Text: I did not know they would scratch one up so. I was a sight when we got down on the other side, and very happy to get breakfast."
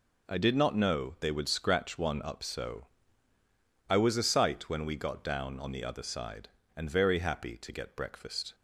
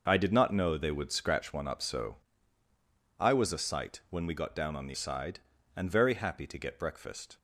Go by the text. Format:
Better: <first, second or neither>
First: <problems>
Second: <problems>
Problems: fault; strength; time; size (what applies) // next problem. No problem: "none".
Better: first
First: none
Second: skips "other"; at 4.9 s